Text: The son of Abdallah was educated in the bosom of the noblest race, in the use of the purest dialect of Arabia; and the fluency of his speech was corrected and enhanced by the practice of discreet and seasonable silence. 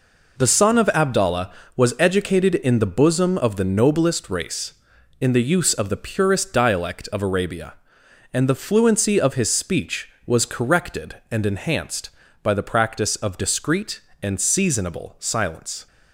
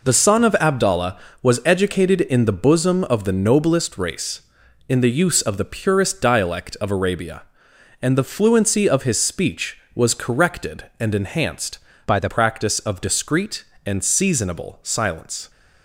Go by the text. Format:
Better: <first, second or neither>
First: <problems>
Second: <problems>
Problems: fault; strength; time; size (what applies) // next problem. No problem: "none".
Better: first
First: none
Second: changes voice from "by" to "the"; from 12.0 to 12.2 s; 0.2 s long